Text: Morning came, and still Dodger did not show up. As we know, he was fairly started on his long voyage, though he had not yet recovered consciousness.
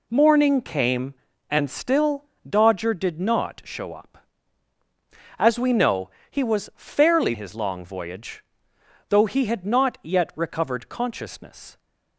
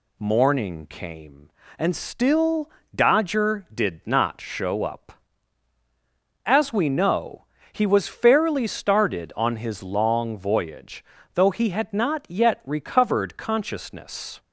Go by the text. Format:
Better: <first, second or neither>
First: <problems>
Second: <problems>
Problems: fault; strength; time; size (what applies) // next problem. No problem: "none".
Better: second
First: pauses between "still" and "Dodger"; slight; at 2.2 s; 0.22 s long // skips "started on"; at 7.3 s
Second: pauses between "still" and "Dodger"; slight; at 2.7 s; 0.24 s long